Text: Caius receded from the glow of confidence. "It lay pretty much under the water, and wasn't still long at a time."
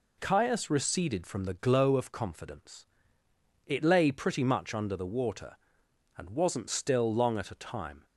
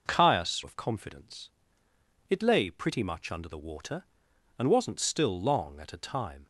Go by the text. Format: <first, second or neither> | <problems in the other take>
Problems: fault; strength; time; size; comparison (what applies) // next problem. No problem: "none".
first | skips "receded from the glow"; at 0.6 s